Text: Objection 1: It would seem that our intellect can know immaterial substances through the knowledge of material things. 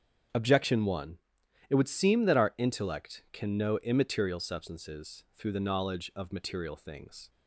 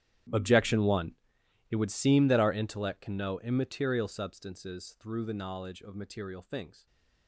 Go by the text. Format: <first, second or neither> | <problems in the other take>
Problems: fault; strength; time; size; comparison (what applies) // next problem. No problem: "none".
first | gets quieter; strong; throughout; 20.5 dB // starts louder than the rest; strong; until 1.8 s; 11 dB; strong in the first // stays silent after the last word; slight; from 6.7 s on; 0.5 s long